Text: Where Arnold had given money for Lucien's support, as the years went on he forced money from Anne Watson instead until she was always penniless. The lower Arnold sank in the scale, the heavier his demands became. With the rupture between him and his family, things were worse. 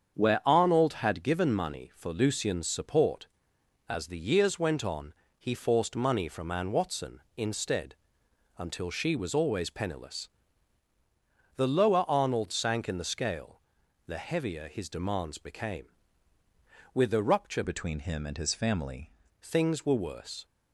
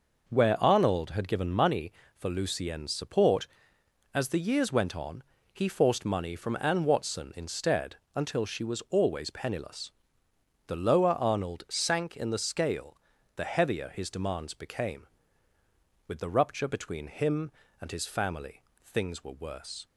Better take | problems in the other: second | starts louder than the rest; strong; until 1.2 s; 7.5 dB // pauses between "on" and "he"; slight; at 5.1 s; 0.24 s long; slight in the second // pauses between "instead" and "until"; noticeable; at 7.9 s; 0.62 s long; slight in the second // changes voice from "between" to "family"; from 17.6 to 19.1 s; 1.5 s long

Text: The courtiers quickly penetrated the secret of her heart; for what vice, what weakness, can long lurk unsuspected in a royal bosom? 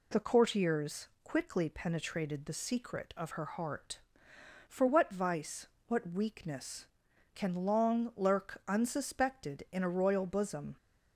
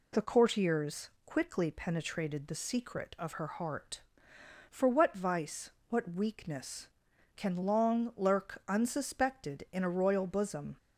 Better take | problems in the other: neither | pauses between "courtiers" and "quickly"; slight; the same in both

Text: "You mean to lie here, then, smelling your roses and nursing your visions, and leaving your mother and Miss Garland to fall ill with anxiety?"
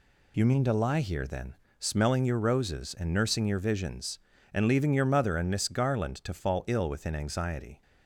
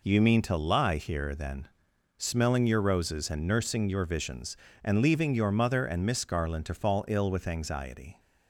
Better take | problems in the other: second | says "within" for "with"; at 6.8 s

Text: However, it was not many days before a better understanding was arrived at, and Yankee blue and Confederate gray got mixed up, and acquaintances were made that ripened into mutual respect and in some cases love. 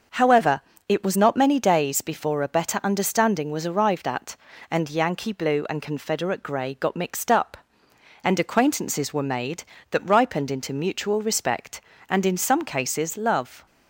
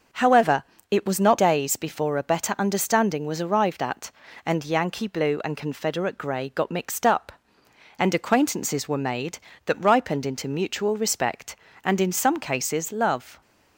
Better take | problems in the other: first | starts louder than the rest; noticeable; until 1.4 s; 6 dB; noticeable in the first // skips "many"; at 1.3 s

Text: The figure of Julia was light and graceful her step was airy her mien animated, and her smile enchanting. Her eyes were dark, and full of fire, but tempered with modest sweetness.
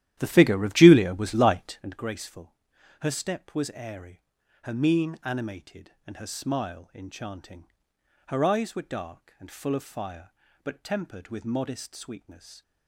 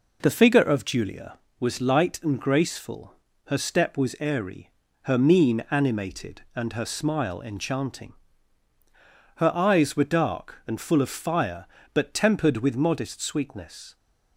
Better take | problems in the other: second | starts louder than the rest; strong; until 2.0 s; 12 dB // pauses between "graceful" and "her"; noticeable; at 2.5 s; 0.48 s long; slight in the second // pauses between "airy" and "her"; at 4.2 s; 0.42 s long; slight in the second

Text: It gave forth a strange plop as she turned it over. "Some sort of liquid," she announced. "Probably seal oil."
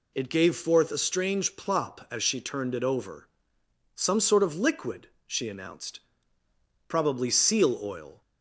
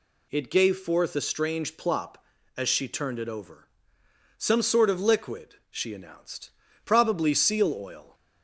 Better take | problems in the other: neither | none

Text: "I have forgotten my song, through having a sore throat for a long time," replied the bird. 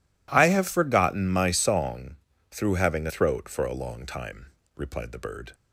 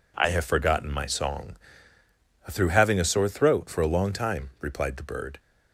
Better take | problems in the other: second | skips "sore"; at 3.0 s

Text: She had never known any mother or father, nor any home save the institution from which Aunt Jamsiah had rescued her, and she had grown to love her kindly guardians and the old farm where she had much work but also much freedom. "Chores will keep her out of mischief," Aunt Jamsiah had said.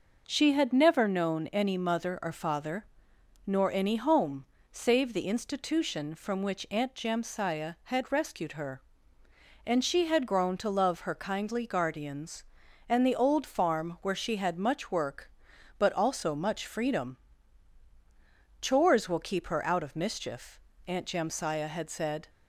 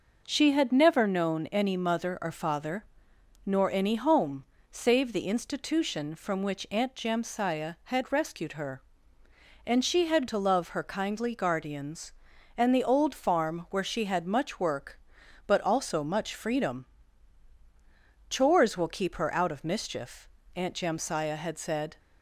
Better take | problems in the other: first | pauses between "home" and "save"; slight; at 4.4 s; 0.26 s long; slight in the first // skips "grown"; at 10.2 s

